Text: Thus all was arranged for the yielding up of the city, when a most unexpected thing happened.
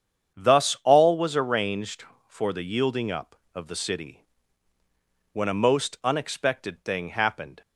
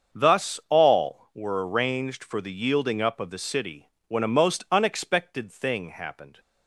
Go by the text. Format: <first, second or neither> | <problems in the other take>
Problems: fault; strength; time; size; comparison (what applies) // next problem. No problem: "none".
first | starts louder than the rest; until 1.2 s; 7 dB; strong in the first // says "were" for "was"; at 1.3 s